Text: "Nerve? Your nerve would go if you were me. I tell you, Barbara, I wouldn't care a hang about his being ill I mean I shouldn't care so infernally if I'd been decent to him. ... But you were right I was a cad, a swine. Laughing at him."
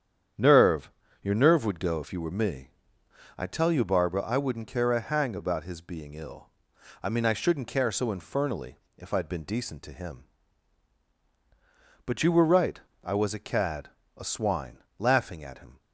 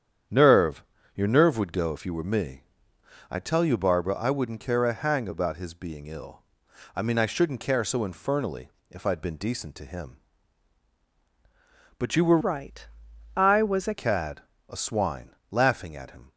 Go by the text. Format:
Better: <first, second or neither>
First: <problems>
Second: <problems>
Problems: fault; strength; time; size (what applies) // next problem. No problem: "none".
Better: first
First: starts louder than the rest; strong; until 1.7 s; 9 dB // pauses between "ill" and "I"; noticeable; at 6.4 s; 0.54 s long // pauses between "infernally" and "if"; slight; at 8.7 s; 0.18 s long // pauses between "right" and "I"; slight; at 12.7 s; 0.21 s long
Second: starts louder than the rest; strong; until 1.6 s; 9 dB // pauses between "ill" and "I"; noticeable; at 6.4 s; 0.54 s long // pauses between "infernally" and "if"; slight; at 8.7 s; 0.18 s long // changes voice from "right" to "a"; from 12.4 to 13.9 s; 1.5 s long // pauses between "right" and "I"; noticeable; at 12.8 s; 0.48 s long